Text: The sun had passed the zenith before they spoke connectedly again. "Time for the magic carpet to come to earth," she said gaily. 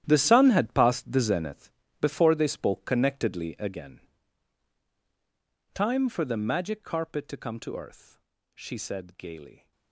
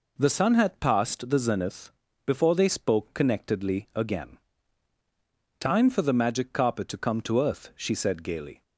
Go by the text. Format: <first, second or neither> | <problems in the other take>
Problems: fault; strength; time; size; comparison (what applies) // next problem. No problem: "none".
second | gets quieter; strong; throughout; 15 dB // pauses between "zenith" and "before"; slight; at 1.7 s; 0.28 s long; slight in the second